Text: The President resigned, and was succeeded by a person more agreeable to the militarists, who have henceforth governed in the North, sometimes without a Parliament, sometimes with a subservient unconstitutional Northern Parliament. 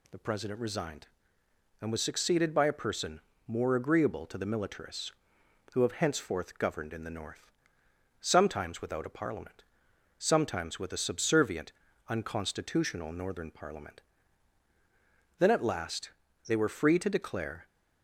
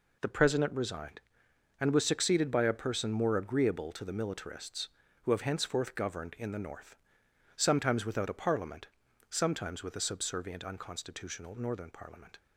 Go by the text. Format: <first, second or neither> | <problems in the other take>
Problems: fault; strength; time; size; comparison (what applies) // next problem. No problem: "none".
second | pauses between "person" and "more"; slight; at 3.1 s; 0.26 s long // pauses between "subservient" and "unconstitutional"; slight; at 11.7 s; 0.36 s long // goes on to say "Then at last they were free to declare"; strong; from 15.3 s on; 2.2 s long